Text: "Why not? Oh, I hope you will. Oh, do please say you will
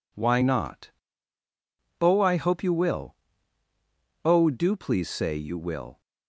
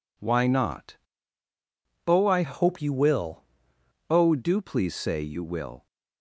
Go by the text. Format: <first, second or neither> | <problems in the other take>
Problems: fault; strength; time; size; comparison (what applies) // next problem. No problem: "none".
first | changes voice from "hope" to "will"; from 2.4 to 3.4 s; 1.0 s long